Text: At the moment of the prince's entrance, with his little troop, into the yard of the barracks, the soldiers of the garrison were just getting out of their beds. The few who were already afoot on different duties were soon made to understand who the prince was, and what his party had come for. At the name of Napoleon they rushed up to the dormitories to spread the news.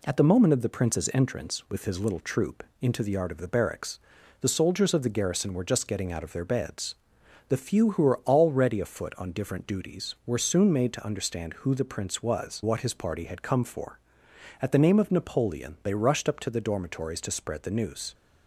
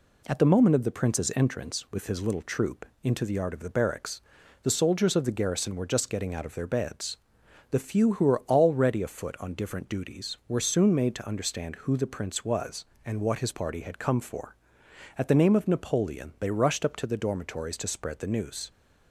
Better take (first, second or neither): second